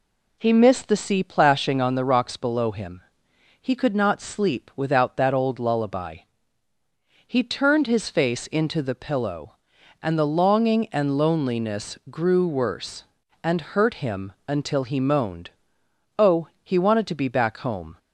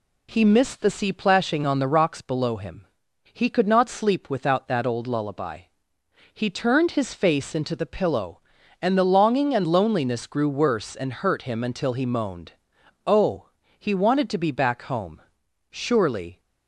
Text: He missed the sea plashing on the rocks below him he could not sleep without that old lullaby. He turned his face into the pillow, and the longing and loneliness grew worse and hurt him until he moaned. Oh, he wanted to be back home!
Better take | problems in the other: first | pauses between "him" and "he"; noticeable; at 2.8 s; 0.48 s long; noticeable in the first // goes on to say "Surely"; noticeable; from 15.7 s on; 0.68 s long

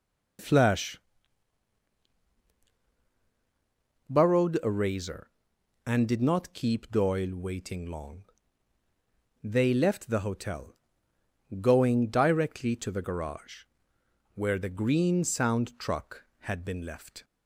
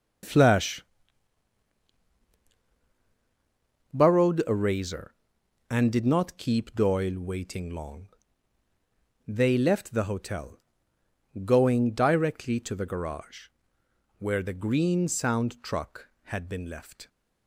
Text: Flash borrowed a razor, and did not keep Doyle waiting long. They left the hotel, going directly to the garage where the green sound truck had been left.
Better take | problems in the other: first | gets quieter; strong; throughout; 10.5 dB // pauses between "Flash" and "borrowed"; strong; at 0.8 s; 3.1 s long; strong in the first // pauses between "garage" and "where"; noticeable; at 13.4 s; 0.70 s long; noticeable in the first

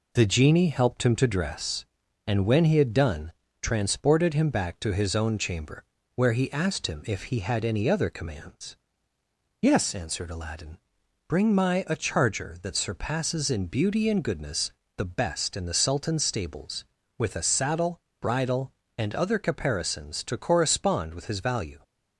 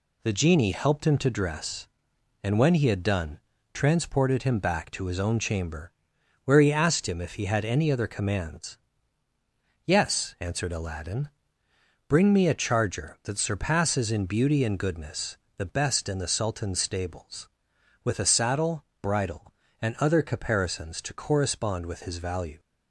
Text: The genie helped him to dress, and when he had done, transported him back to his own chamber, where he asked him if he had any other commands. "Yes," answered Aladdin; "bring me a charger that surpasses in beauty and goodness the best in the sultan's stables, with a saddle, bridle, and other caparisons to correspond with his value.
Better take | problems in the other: second | says "my" for "me"; at 11.5 s // pauses between "goodness" and "the"; slight; at 14.6 s; 0.28 s long; slight in the second

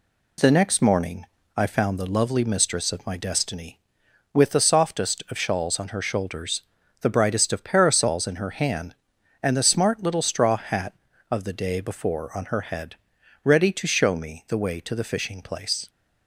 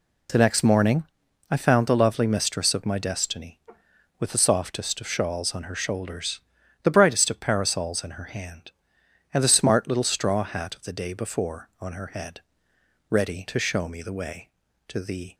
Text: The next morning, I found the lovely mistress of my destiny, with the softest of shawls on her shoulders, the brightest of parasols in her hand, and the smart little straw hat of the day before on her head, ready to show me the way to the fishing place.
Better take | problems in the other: first | stops before "fishing place"; at 15.3 s

